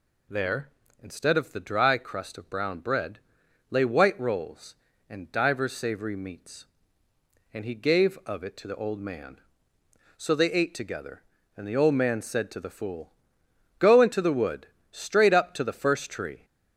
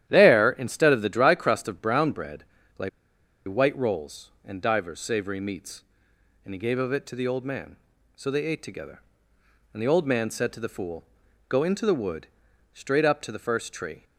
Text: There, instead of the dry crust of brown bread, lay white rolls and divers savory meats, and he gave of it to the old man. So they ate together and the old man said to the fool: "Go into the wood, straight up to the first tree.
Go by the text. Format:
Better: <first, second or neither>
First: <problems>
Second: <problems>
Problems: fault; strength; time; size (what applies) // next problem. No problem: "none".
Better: first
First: none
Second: starts louder than the rest; strong; until 1.0 s; 11.5 dB // pauses between "lay" and "white"; noticeable; at 2.8 s; 0.58 s long